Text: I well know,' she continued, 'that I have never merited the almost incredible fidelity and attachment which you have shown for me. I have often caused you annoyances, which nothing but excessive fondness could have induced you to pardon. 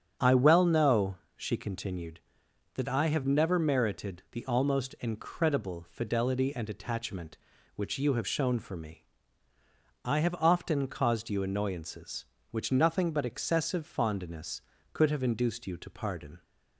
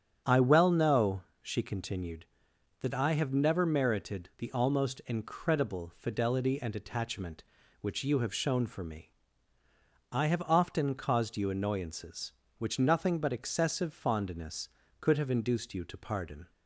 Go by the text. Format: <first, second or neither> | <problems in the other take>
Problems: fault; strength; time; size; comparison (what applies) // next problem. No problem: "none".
neither | starts louder than the rest; strong; the same in both